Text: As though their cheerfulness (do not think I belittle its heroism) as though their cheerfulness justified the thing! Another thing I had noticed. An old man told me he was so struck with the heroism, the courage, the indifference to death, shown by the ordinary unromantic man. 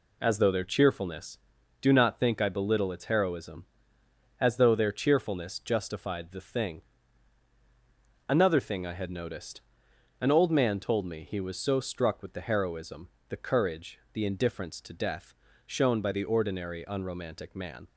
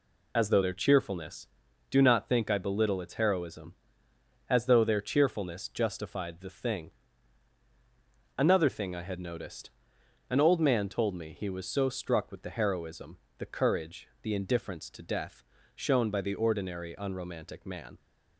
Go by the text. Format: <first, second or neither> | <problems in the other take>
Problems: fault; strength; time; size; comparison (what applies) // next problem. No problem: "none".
first | loses the start of "As"; at 0.3 s; 35 ms